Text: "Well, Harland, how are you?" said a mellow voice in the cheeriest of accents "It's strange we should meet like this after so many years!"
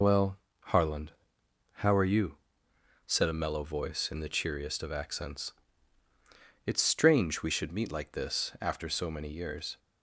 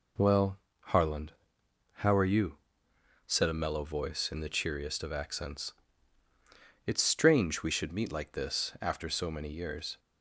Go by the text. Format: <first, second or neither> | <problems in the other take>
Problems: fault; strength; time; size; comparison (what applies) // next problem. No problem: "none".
second | loses the start of "Well"; at 0.0 s; 30 ms // pauses between "accents" and "It's"; at 5.5 s; 1.1 s long; also in the second